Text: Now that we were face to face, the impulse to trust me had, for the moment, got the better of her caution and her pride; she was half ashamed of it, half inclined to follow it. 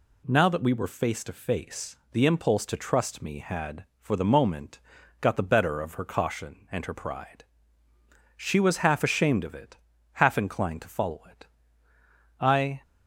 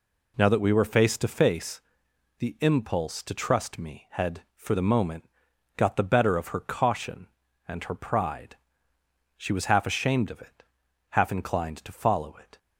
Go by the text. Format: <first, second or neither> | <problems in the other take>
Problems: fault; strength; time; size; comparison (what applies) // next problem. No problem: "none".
second | goes on to say "I"; slight; from 12.3 s on; 0.42 s long